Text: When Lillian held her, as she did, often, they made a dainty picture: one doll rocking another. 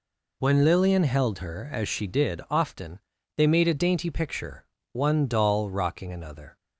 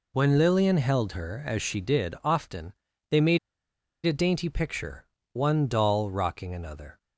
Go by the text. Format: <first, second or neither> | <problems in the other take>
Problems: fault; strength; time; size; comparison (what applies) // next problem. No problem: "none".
first | pauses between "made" and "a"; noticeable; at 3.3 s; 0.67 s long